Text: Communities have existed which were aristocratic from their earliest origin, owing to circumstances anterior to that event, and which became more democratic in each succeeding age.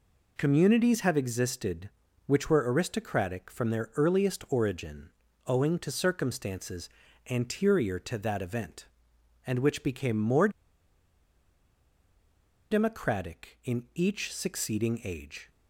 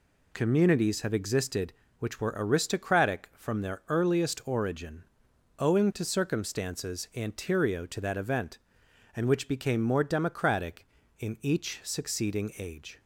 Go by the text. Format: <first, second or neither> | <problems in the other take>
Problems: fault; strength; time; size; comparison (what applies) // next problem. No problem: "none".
second | pauses between "circumstances" and "anterior"; at 6.8 s; 0.42 s long // pauses between "more" and "democratic"; strong; at 10.4 s; 2.2 s long